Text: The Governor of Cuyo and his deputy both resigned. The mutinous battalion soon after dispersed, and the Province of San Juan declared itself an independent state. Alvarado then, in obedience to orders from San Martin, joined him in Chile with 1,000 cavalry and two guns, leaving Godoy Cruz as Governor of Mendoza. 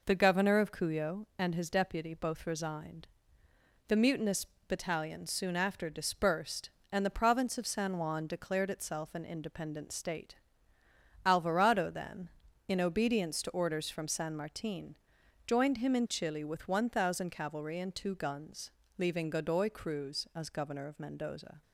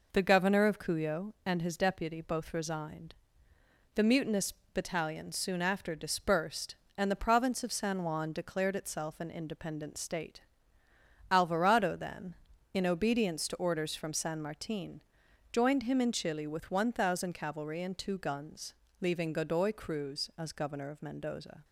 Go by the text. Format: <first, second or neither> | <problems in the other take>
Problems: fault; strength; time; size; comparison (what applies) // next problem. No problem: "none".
neither | pauses between "mutinous" and "battalion"; slight; the same in both